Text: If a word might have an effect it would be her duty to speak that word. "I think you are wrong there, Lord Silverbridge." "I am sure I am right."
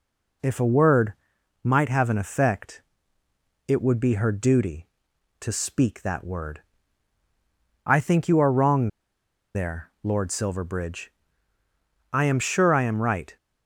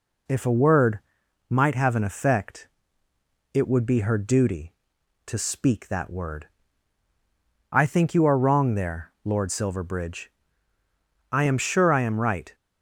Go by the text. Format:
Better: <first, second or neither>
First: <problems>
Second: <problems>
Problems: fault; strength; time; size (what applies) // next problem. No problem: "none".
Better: second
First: pauses between "word" and "might"; noticeable; at 1.1 s; 0.50 s long // pauses between "effect" and "it"; noticeable; at 2.8 s; 0.86 s long // pauses between "wrong" and "there"; noticeable; at 8.8 s; 0.67 s long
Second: pauses between "word" and "might"; noticeable; at 0.9 s; 0.50 s long // pauses between "effect" and "it"; noticeable; at 2.6 s; 0.86 s long